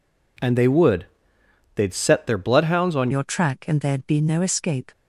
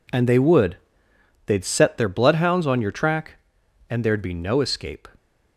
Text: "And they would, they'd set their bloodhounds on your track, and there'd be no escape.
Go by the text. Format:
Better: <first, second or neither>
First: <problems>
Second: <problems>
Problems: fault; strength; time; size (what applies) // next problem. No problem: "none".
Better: second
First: changes voice at "your"; from 3.1 s on; 1.8 s long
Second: none